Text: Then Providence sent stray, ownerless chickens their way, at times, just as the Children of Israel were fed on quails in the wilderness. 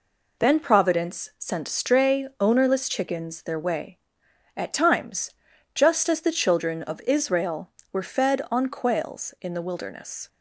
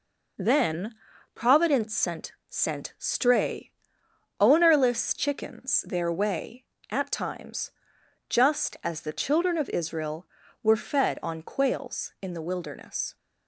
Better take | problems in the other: first | pauses between "Then" and "Providence"; at 0.9 s; 0.40 s long // says "sent" twice; at 2.4 s

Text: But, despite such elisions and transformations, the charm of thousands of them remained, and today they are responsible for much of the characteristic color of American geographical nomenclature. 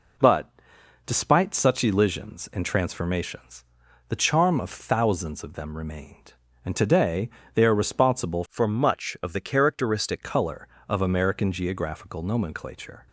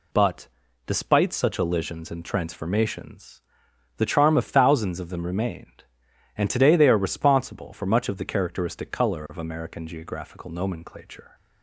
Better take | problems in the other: second | pauses between "today" and "they"; slight; at 7.2 s; 0.24 s long // changes voice from "for" to "characteristic"; from 8.4 to 10.2 s; 1.8 s long

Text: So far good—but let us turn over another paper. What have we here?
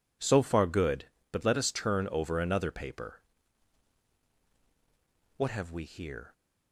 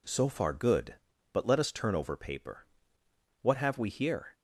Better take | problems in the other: first | skips "another"; at 2.1 s

